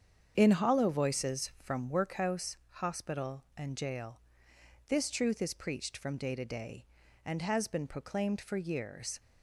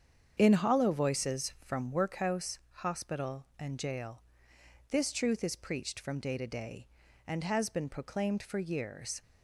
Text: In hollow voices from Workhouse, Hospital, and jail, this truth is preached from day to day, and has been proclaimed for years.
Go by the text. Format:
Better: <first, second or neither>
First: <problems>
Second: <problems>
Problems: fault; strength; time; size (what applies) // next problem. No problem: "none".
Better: neither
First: starts louder than the rest; strong; until 1.3 s; 7.5 dB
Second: starts louder than the rest; strong; until 1.3 s; 7.5 dB